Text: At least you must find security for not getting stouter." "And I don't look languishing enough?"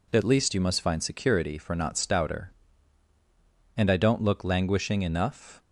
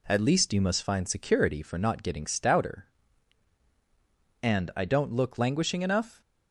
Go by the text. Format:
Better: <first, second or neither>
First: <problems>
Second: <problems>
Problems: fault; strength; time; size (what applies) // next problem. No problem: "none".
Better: second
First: skips "getting"; at 1.9 s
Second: none